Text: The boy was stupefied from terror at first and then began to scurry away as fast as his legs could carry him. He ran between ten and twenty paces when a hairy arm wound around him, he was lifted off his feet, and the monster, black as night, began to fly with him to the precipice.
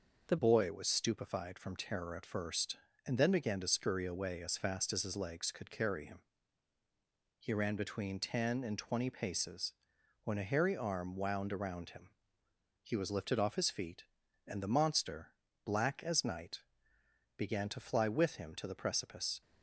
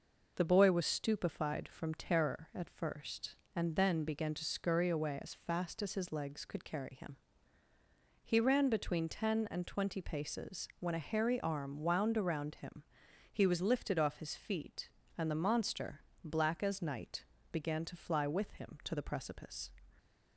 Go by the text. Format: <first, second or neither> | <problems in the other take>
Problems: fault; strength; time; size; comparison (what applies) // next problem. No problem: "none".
second | changes voice at "boy"; from 0.3 s on; 19.1 s long // pauses between "paces" and "when"; noticeable; at 9.7 s; 0.50 s long